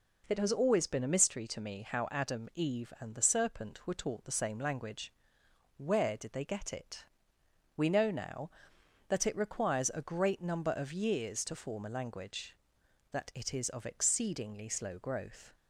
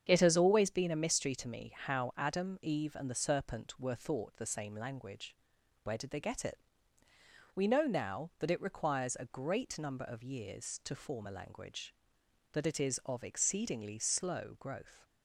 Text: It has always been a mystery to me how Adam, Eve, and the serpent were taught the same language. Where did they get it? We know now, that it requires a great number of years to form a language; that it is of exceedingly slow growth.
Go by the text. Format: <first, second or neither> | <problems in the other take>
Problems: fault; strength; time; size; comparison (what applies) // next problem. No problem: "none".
first | starts louder than the rest; strong; until 1.0 s; 8 dB // says "thought" for "taught"; at 3.9 s